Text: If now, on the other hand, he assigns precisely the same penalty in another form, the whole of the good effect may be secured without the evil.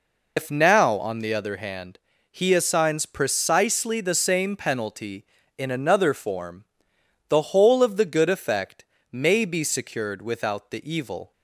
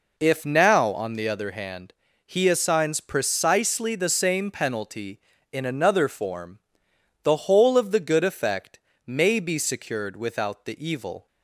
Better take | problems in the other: second | loses the start of "If"; at 0.3 s; 125 ms // pauses between "effect" and "may"; slight; at 8.8 s; 0.26 s long; slight in the second

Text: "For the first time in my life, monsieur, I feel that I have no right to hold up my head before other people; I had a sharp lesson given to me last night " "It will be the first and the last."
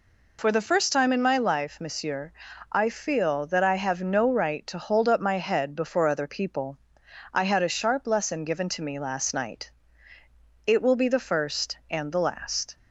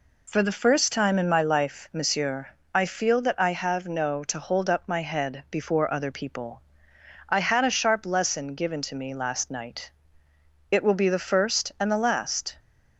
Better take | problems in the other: first | skips "right"; at 4.2 s

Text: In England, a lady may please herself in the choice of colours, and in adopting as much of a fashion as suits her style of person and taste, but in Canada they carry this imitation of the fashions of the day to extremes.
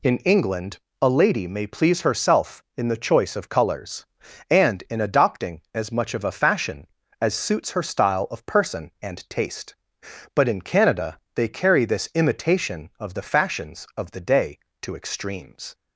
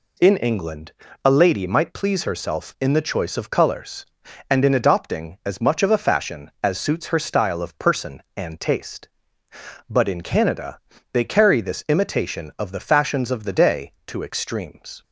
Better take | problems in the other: first | says "might" for "may"; at 1.6 s // pauses between "Canada" and "they"; slight; at 10.7 s; 0.32 s long; slight in the first

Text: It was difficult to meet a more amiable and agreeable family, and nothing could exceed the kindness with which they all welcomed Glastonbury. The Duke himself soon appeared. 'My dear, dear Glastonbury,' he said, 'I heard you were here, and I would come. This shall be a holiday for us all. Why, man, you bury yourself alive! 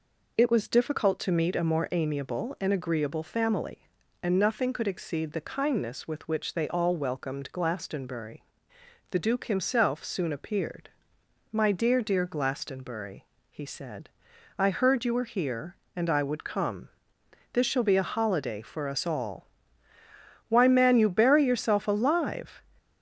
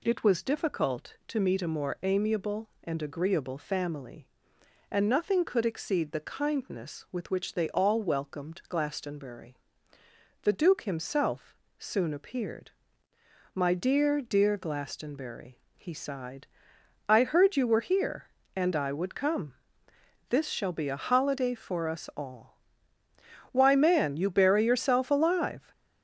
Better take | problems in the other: first | pauses between "himself" and "soon"; slight; at 11.5 s; 0.24 s long // says "sighed" for "said"; at 15.9 s

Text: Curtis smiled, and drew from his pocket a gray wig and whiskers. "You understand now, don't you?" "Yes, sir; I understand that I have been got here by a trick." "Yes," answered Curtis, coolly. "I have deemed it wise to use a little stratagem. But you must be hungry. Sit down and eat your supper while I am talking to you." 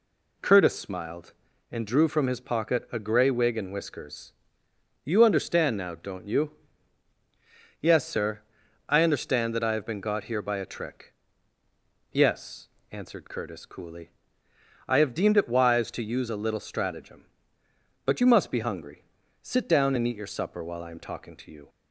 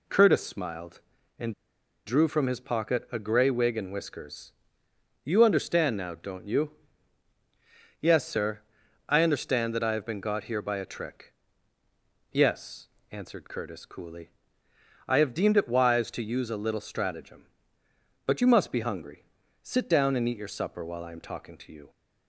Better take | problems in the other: first | pauses between "and" and "drew"; noticeable; at 1.5 s; 0.52 s long

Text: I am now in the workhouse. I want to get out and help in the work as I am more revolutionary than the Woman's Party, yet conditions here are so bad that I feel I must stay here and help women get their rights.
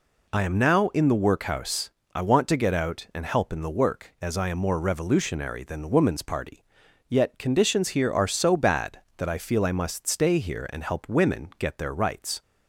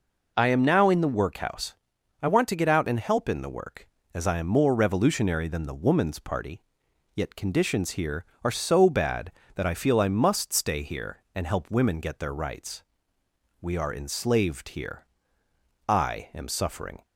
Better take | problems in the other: first | goes on to say "We are enslaved here I am suffering"; strong; from 13.6 s on; 3.4 s long

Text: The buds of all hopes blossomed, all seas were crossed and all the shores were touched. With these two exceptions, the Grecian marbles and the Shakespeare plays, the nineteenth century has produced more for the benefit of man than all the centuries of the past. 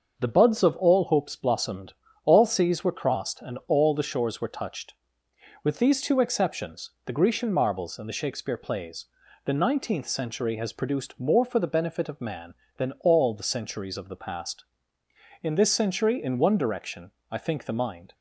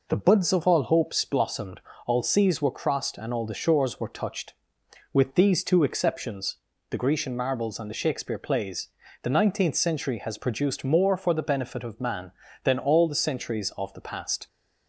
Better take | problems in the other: second | starts louder than the rest; until 1.1 s; 6.5 dB // goes on to say "In this century in one direction I think the mind"; strong; from 15.4 s on; 2.7 s long

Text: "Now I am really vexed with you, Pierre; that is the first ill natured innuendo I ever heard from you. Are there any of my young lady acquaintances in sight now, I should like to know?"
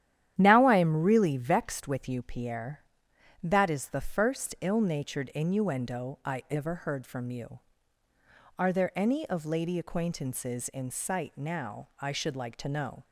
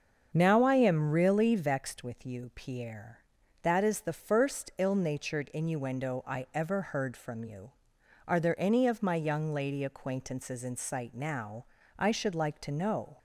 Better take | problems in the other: second | starts louder than the rest; strong; until 1.3 s; 11 dB; also in the second // skips "my young"; at 9.4 s

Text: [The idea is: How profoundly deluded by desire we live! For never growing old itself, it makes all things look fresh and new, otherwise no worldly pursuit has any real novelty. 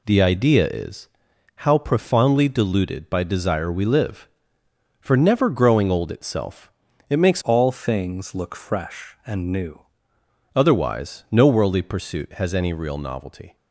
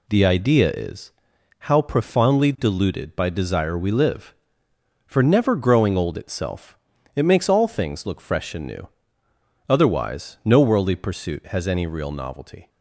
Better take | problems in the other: second | changes voice from "all" to "new"; from 7.4 to 9.8 s; 2.4 s long

